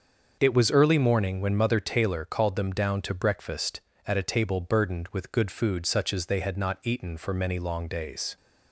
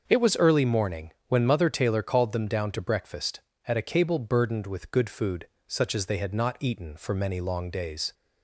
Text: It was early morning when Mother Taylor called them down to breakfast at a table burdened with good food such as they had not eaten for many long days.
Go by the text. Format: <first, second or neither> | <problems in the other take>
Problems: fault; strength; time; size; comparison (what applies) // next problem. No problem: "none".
first | starts louder than the rest; until 1.0 s; 6.5 dB; also in the first // pauses between "morning" and "when"; slight; at 1.1 s; 0.16 s long // says "cable" for "table"; at 3.8 s // pauses between "food" and "such"; slight; at 5.4 s; 0.18 s long